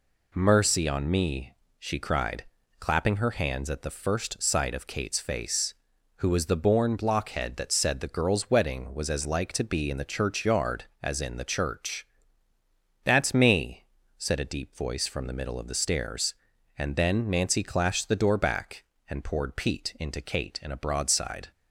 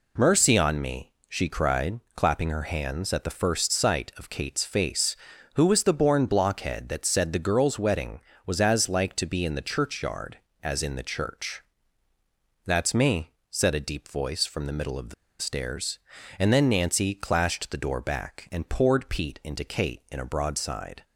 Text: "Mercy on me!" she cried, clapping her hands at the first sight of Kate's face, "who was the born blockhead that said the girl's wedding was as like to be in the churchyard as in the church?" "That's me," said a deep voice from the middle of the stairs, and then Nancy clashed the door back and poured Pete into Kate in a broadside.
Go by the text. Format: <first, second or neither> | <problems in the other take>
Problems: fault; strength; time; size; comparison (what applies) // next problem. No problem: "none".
first | pauses between "the" and "stairs"; slight; at 15.1 s; 0.27 s long